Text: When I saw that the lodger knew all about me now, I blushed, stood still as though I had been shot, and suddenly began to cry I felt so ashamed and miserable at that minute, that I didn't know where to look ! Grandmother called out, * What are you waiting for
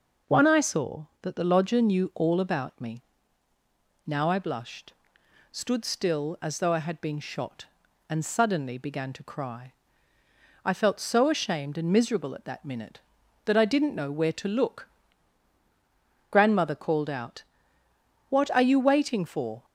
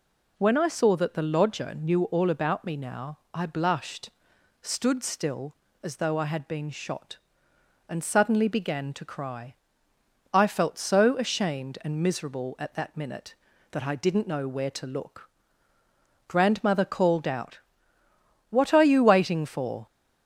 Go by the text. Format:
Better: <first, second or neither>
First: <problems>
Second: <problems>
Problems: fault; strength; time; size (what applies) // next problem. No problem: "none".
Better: second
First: says "One" for "When"; at 0.2 s // pauses between "me" and "now"; at 3.0 s; 1.0 s long // pauses between "cry" and "I"; noticeable; at 9.7 s; 0.92 s long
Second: pauses between "cry" and "I"; noticeable; at 9.5 s; 0.80 s long